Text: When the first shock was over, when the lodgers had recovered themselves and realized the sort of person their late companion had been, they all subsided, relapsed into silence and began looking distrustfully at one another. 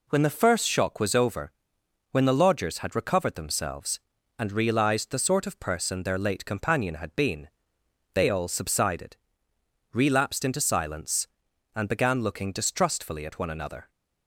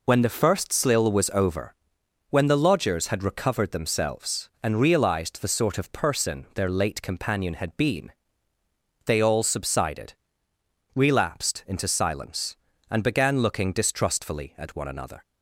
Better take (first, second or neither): first